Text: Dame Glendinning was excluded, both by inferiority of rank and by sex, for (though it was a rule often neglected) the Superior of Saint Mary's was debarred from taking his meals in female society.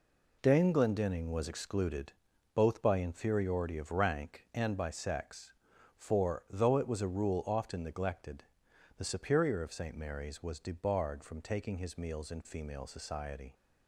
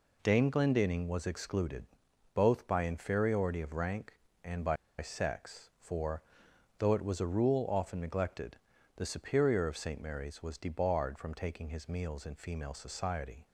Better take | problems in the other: first | pauses between "by" and "sex"; slight; at 4.7 s; 0.23 s long

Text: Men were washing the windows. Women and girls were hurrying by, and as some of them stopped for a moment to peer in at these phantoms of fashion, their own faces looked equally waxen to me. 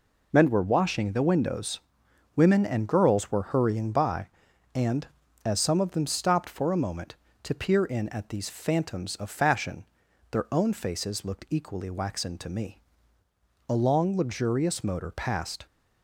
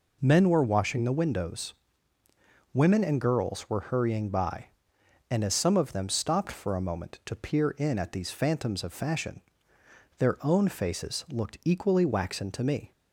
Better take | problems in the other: second | goes on to say "A long luxurious motor passed"; strong; from 13.6 s on; 1.9 s long

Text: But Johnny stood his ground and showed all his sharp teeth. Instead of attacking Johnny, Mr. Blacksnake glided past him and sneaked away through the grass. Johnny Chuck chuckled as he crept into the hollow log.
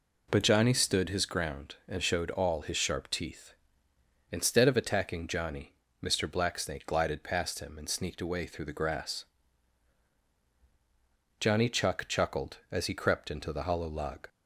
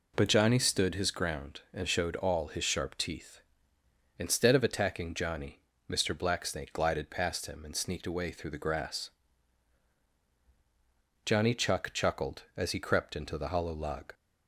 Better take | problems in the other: neither | none

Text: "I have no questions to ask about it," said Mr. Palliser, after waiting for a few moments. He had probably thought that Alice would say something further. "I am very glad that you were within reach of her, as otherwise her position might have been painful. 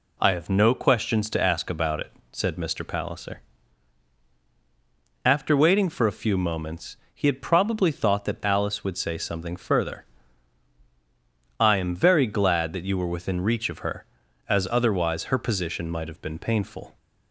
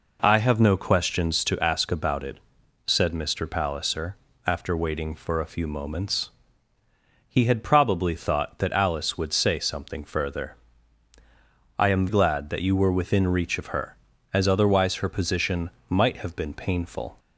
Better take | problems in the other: first | skips "very"; at 12.0 s // pauses between "position" and "might"; slight; at 15.7 s; 0.18 s long

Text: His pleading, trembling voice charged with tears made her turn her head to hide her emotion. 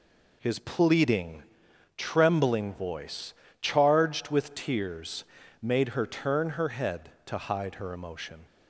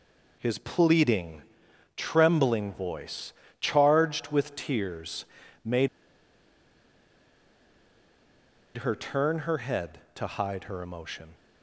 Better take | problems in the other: first | pauses between "voice" and "charged"; slight; at 3.3 s; 0.26 s long; slight in the first // pauses between "tears" and "made"; at 5.2 s; 0.40 s long; also in the first // pauses between "made" and "her"; strong; at 5.8 s; 2.8 s long

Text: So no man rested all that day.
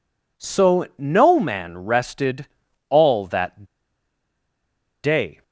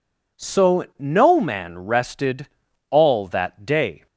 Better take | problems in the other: second | pauses between "rested" and "all"; at 2.4 s; 0.42 s long; also in the second // pauses between "that" and "day"; strong; at 3.6 s; 1.4 s long

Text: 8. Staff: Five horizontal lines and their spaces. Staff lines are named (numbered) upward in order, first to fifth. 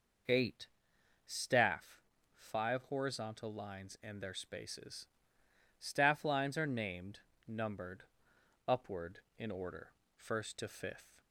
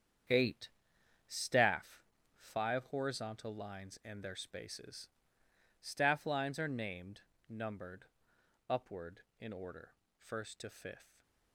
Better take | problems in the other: first | gets quieter; strong; throughout; 10 dB // stays silent after the last word; slight; from 11.0 s on; 0.5 s long

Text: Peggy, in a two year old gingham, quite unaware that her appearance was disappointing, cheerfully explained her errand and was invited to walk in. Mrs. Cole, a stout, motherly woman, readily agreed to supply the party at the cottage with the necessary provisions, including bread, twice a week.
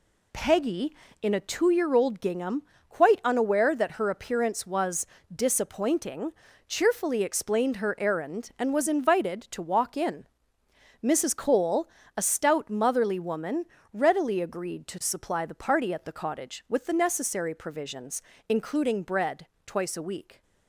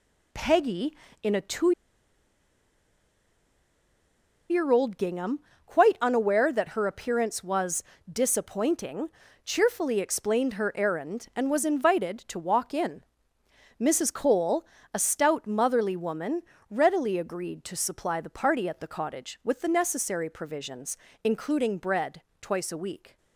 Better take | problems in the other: first | pauses between "two" and "year"; strong; at 1.7 s; 2.7 s long // pauses between "was" and "disappointing"; slight; at 7.8 s; 0.28 s long; slight in the first

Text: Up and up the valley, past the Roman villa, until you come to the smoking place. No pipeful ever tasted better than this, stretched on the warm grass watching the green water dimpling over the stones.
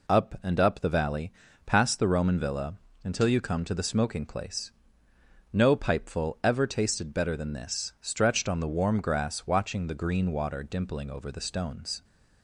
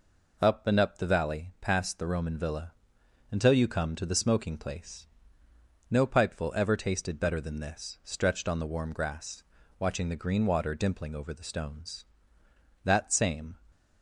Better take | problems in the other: first | pauses between "grass" and "watching"; slight; at 9.4 s; 0.36 s long // goes on to say "That same"; noticeable; from 12.8 s on; 0.74 s long

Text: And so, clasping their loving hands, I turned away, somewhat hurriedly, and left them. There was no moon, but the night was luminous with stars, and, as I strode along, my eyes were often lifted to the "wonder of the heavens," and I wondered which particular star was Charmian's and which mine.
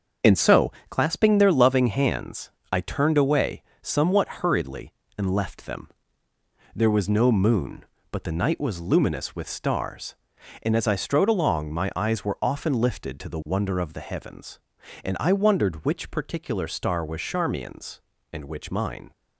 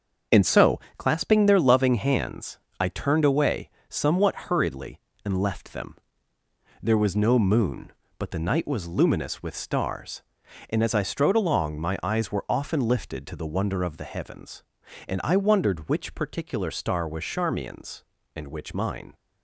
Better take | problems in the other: neither | starts louder than the rest; the same in both

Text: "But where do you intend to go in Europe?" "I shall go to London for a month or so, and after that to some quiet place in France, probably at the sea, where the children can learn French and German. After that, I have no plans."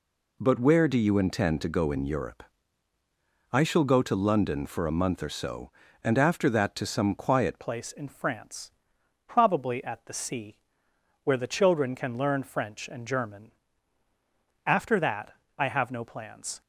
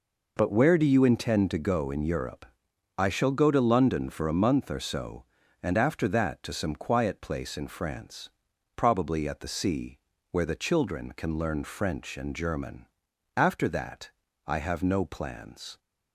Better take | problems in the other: second | changes voice at "place"; from 7.6 s on; 9.0 s long

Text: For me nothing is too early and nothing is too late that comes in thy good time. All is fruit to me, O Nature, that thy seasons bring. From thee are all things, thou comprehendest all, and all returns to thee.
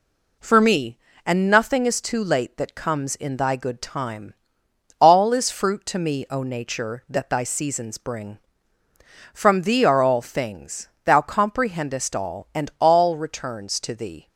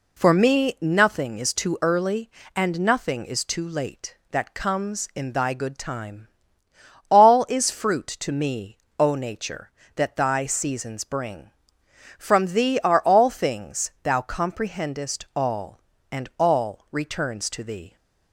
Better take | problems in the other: second | skips "nothing is too early"; at 1.1 s

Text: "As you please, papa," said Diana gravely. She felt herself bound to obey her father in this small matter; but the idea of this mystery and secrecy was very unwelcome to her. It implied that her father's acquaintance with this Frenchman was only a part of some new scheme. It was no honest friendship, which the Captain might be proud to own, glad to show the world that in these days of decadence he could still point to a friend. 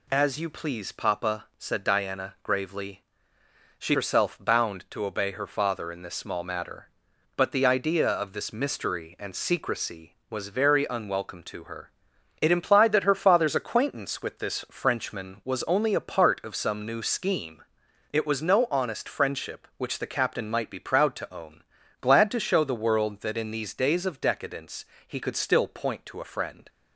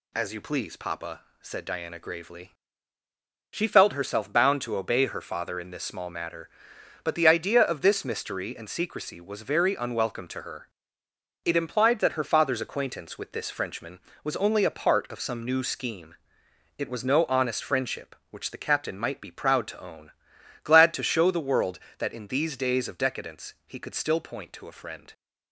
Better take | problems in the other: second | skips "felt"; at 3.9 s // pauses between "decadence" and "he"; slight; at 24.8 s; 0.22 s long

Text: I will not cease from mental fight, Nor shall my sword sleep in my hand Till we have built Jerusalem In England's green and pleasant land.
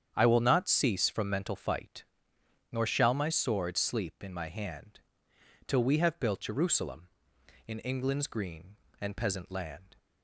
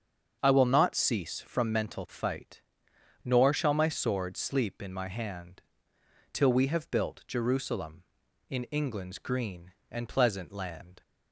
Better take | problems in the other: second | starts louder than the rest; strong; until 1.1 s; 8.5 dB; also in the second // pauses between "hand" and "Till"; noticeable; at 5.0 s; 0.66 s long; noticeable in the second // says "peasant" for "pleasant"; at 9.1 s

